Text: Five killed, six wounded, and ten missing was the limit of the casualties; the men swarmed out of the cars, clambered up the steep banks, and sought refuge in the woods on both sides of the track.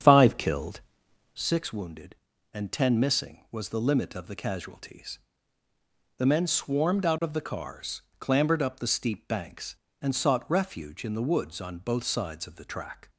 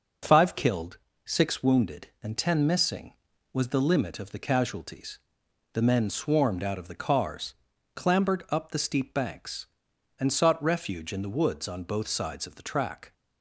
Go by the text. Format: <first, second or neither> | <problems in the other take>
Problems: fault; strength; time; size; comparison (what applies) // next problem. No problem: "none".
second | starts louder than the rest; strong; until 1.4 s; 8.5 dB